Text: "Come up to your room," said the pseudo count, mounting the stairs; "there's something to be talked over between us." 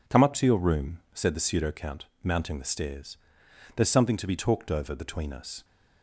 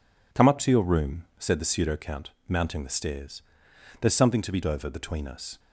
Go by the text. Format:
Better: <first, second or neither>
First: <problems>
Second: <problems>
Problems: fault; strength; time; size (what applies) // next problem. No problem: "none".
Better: first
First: none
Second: skips "talked"; at 4.6 s